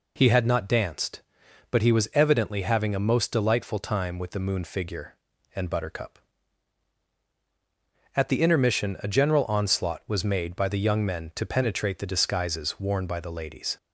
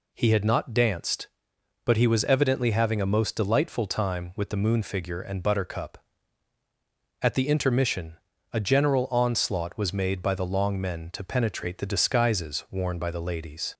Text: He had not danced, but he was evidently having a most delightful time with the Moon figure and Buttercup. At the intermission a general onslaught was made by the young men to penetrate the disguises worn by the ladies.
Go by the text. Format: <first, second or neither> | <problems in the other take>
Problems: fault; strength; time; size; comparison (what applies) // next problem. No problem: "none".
first | pauses between "intermission" and "a"; at 8.1 s; 0.38 s long // says "long" for "young"; at 10.4 s